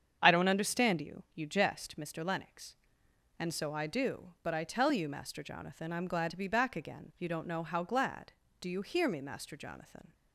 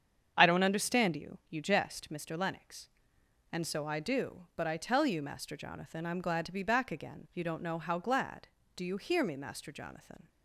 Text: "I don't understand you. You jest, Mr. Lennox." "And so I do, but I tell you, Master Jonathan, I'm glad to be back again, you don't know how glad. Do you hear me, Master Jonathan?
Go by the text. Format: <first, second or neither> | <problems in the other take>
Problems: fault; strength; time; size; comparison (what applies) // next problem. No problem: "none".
neither | starts louder than the rest; strong; the same in both